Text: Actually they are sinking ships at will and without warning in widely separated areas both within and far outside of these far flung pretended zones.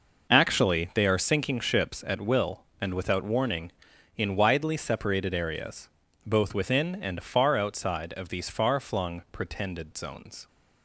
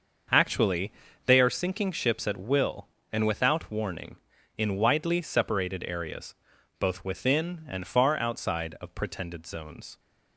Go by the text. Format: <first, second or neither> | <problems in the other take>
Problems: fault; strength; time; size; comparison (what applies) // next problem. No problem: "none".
first | starts louder than the rest; until 1.6 s; 6.5 dB // pauses between "Actually" and "they"; slight; at 0.9 s; 0.34 s long // pauses between "areas" and "both"; at 6.3 s; 0.44 s long; also in the first // skips "these far flung"; at 8.9 s